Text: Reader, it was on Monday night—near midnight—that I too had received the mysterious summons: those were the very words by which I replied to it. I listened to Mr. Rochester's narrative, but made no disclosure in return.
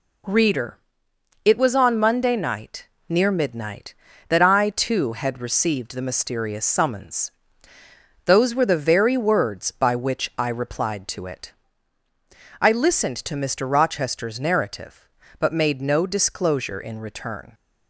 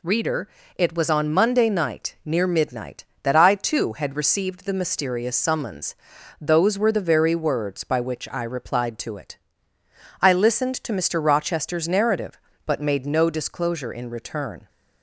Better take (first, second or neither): neither